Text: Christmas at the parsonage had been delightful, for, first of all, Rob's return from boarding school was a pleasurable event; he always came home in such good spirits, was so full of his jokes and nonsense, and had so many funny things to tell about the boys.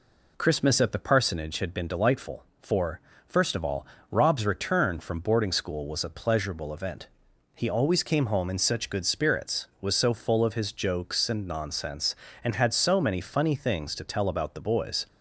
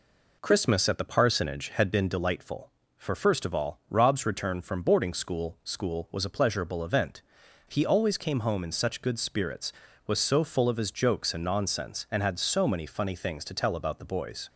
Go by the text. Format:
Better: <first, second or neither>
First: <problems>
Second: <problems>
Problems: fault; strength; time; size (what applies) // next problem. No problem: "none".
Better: first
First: none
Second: says "school" twice; at 5.6 s